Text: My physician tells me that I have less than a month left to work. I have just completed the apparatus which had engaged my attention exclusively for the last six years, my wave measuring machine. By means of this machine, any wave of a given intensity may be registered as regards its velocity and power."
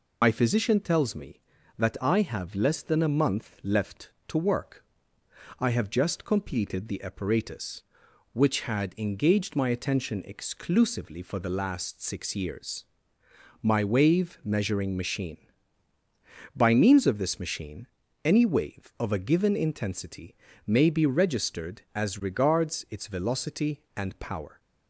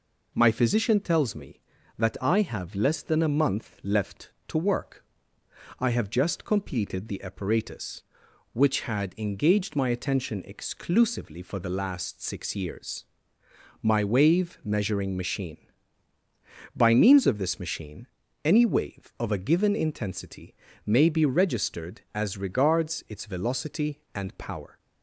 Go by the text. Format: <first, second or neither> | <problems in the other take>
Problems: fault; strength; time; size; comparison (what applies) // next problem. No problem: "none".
second | loses the start of "My"; at 0.2 s; 70 ms // pauses between "intensity" and "may"; slight; at 20.3 s; 0.32 s long; slight in the second